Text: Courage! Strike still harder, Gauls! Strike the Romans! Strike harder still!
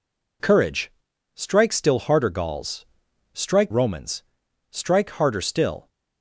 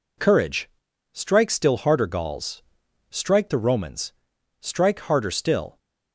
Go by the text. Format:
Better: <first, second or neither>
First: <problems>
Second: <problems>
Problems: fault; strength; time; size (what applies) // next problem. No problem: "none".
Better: second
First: skips "the"; at 3.7 s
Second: none